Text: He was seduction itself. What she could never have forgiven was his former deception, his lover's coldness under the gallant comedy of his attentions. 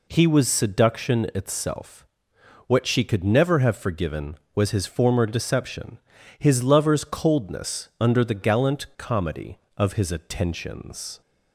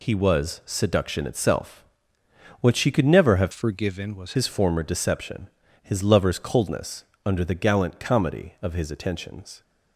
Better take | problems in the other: first | changes voice from "forgiven" to "was"; from 3.5 to 4.3 s; 0.8 s long // pauses between "coldness" and "under"; slight; at 7.0 s; 0.22 s long

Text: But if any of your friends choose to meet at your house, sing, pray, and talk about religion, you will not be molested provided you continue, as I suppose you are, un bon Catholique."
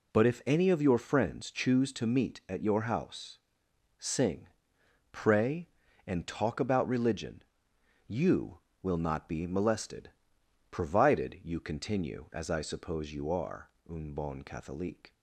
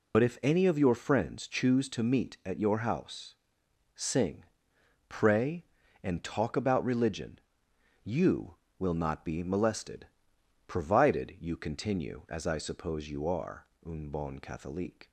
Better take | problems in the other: first | loses the start of "But"; at 0.1 s; 55 ms // pauses between "molested" and "provided"; noticeable; at 10.0 s; 0.60 s long; noticeable in the first

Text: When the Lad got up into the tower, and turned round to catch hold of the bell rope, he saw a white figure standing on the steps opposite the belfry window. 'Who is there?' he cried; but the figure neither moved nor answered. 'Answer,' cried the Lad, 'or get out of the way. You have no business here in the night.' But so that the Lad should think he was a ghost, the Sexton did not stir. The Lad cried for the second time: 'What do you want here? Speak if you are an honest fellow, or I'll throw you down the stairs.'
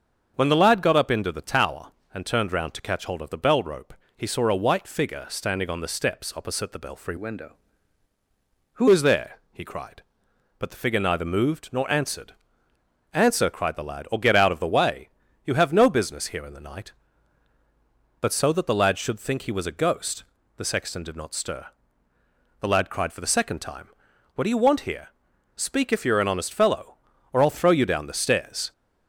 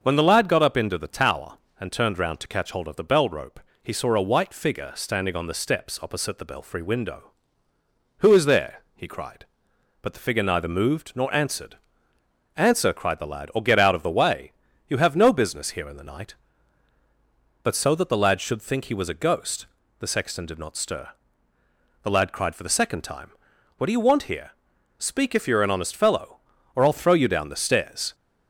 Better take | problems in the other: second | starts louder than the rest; strong; until 1.3 s; 7 dB; also in the second // changes voice from "window" to "Who"; from 7.1 to 8.8 s; 1.7 s long

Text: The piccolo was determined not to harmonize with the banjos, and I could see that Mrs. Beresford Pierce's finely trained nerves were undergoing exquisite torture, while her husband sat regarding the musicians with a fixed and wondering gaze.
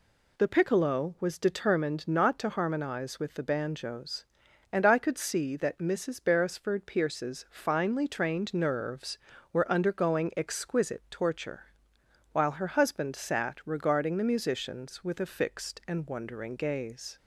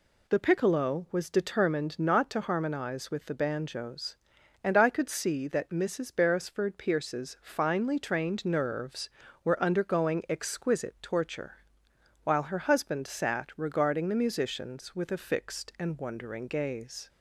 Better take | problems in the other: neither | none

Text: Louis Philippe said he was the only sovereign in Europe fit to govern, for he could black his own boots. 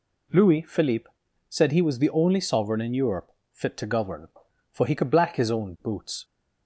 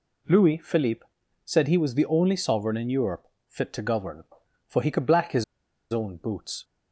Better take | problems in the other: first | pauses between "Philippe" and "said"; at 1.0 s; 0.40 s long; also in the first // pauses between "Europe" and "fit"; slight; at 3.2 s; 0.20 s long; slight in the first // pauses between "his" and "own"; noticeable; at 5.4 s; 0.47 s long

